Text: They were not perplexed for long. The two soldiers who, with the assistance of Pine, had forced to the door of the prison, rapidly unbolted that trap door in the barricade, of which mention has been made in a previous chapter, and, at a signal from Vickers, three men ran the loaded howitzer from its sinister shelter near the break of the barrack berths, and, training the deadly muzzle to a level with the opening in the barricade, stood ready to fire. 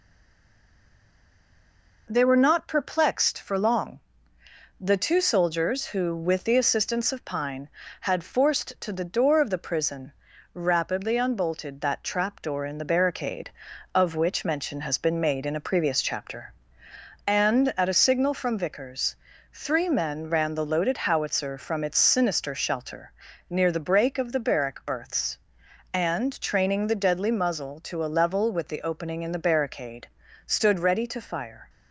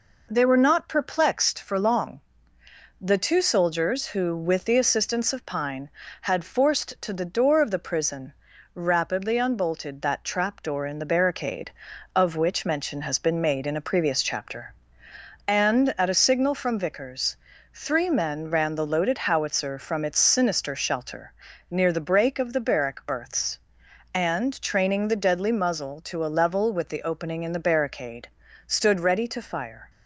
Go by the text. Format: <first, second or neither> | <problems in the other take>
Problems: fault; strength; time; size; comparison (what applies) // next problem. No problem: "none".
second | stays silent before the first word; noticeable; until 2.0 s; 2.0 s long // pauses between "shelter" and "near"; at 23.1 s; 0.38 s long; also in the second